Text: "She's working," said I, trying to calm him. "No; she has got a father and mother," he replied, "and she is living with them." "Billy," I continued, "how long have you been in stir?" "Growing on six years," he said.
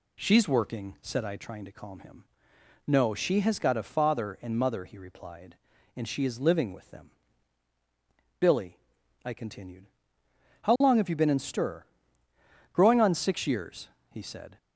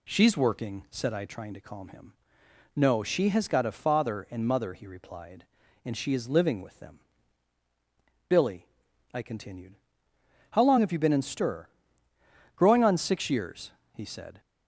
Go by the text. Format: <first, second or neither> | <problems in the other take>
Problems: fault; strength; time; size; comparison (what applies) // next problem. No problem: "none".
neither | none